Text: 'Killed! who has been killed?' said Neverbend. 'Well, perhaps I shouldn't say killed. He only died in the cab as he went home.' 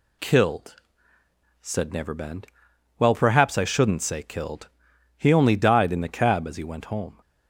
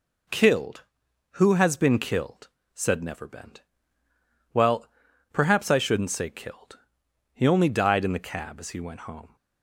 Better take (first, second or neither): second